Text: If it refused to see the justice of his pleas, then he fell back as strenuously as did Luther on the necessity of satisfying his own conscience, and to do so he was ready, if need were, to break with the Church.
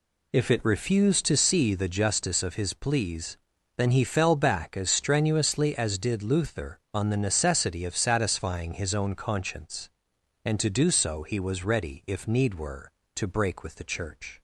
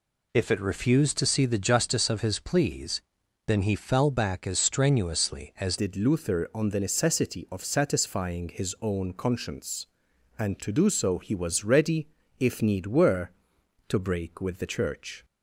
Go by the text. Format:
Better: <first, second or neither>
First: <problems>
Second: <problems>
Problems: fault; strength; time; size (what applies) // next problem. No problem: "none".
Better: first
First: none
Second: changes voice at "did"; from 5.7 s on; 9.5 s long